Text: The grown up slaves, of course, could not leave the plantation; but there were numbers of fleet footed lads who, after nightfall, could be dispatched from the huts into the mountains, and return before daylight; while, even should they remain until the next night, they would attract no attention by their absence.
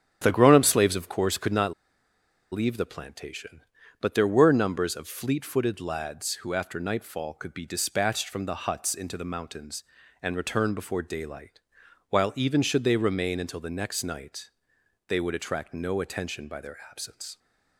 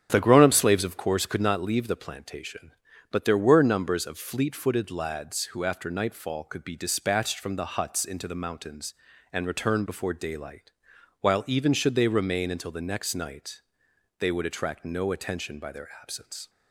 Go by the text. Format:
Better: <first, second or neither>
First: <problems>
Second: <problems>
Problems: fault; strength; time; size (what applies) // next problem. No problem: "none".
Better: second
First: starts louder than the rest; strong; until 1.2 s; 8.5 dB // pauses between "not" and "leave"; noticeable; at 1.7 s; 0.78 s long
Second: starts louder than the rest; strong; until 1.1 s; 8 dB